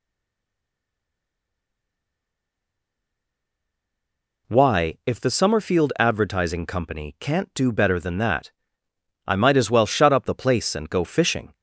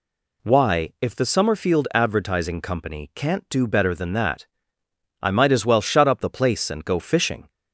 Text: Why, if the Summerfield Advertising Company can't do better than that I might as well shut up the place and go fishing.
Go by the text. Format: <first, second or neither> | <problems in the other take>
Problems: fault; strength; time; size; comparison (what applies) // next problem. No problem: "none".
second | stays silent before the first word; strong; until 4.4 s; 4.4 s long // pauses between "that" and "I"; noticeable; at 8.5 s; 0.76 s long; noticeable in the second